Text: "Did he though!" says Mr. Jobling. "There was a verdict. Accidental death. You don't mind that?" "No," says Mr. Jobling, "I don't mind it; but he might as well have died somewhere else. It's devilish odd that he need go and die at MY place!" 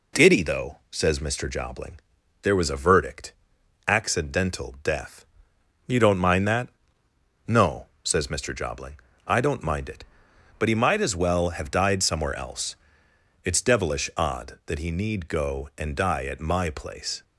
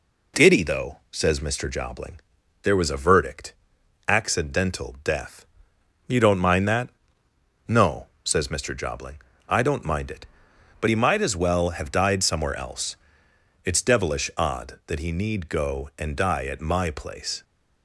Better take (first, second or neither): neither